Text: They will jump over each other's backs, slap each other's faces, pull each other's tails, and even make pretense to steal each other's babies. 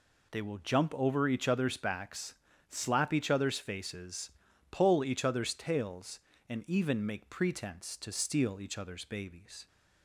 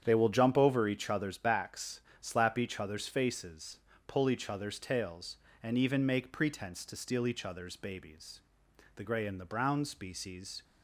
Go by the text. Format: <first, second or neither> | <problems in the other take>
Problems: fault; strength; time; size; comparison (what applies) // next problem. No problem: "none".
first | starts louder than the rest; strong; until 1.0 s; 9 dB // goes on to say "The gray and the brown species"; strong; from 8.9 s on; 1.6 s long